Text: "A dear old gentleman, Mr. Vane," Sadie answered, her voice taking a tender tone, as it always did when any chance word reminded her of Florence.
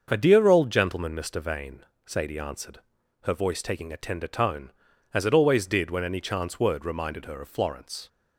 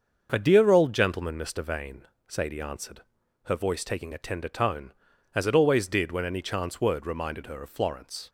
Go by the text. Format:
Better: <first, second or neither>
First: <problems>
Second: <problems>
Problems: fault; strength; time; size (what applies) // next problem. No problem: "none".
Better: neither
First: starts louder than the rest; until 1.1 s; 6.5 dB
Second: starts louder than the rest; until 1.3 s; 6.5 dB